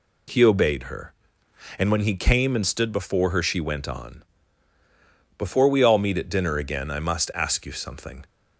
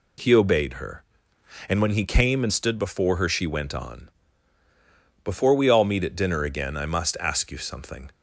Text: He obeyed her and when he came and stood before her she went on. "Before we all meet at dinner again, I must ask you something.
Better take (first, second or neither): neither